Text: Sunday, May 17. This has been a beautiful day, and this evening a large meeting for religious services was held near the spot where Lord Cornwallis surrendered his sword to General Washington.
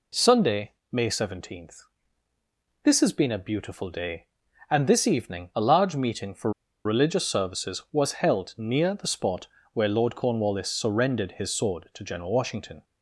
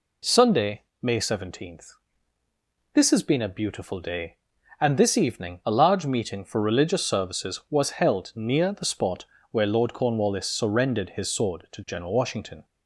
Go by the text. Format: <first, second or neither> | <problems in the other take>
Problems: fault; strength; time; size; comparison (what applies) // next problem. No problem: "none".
second | pauses between "for" and "religious"; slight; at 6.5 s; 0.33 s long // pauses between "spot" and "where"; slight; at 9.4 s; 0.26 s long; slight in the second